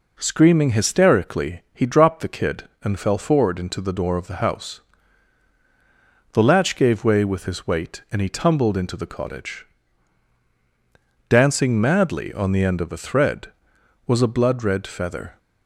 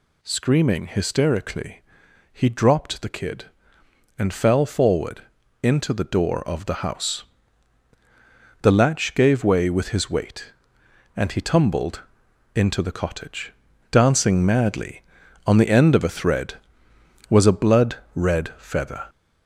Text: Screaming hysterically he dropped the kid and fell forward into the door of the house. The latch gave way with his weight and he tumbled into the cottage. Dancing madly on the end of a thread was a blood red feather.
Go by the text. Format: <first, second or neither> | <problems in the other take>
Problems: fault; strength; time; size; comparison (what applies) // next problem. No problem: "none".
first | gets louder; throughout; 4 dB // pauses between "hysterically" and "he"; noticeable; at 1.8 s; 0.50 s long // pauses between "forward" and "into"; at 5.2 s; 0.40 s long // pauses between "tumbled" and "into"; noticeable; at 12.0 s; 0.54 s long // pauses between "blood" and "red"; slight; at 17.9 s; 0.18 s long